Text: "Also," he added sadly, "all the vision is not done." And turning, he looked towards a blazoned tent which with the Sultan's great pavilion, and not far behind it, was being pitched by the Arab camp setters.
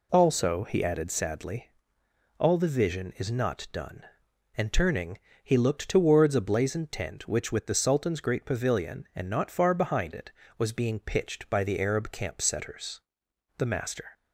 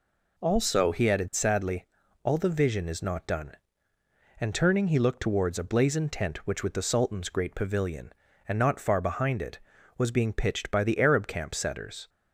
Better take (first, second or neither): second